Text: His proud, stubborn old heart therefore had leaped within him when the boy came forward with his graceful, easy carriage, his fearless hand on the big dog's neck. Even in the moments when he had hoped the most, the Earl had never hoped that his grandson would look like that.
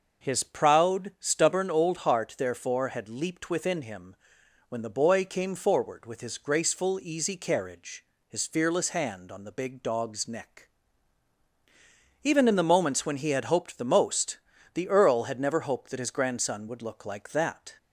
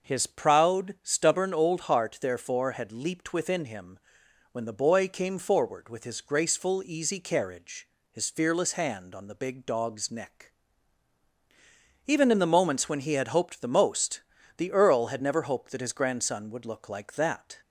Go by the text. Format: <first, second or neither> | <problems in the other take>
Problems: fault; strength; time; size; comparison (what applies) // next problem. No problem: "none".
neither | starts louder than the rest; noticeable; the same in both // pauses between "him" and "when"; noticeable; the same in both